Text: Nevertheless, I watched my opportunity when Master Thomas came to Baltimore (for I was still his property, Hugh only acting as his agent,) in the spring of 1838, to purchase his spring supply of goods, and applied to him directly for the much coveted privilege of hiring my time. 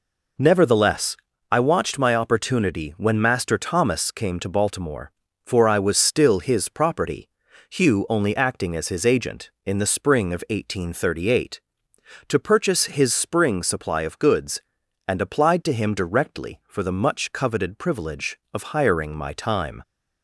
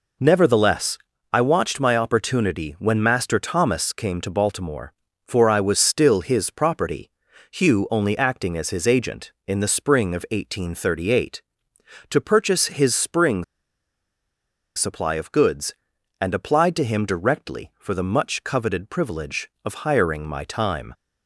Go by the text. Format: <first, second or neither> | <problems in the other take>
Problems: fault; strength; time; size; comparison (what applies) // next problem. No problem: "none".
first | pauses between "spring" and "supply"; strong; at 13.4 s; 1.3 s long